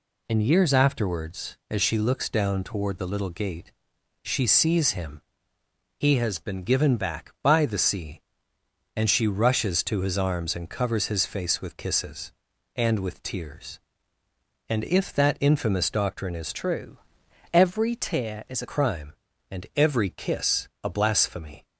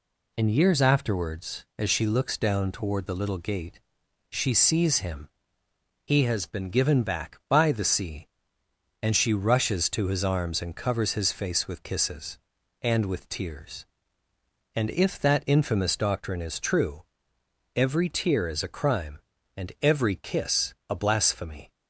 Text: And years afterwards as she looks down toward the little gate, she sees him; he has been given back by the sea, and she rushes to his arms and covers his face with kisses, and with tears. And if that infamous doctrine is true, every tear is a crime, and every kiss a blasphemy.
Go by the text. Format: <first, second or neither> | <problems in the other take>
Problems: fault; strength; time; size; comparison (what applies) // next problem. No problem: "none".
second | changes voice from "true" to "a"; from 16.5 to 18.6 s; 2.1 s long // pauses between "kiss" and "a"; slight; at 20.6 s; 0.16 s long; slight in the second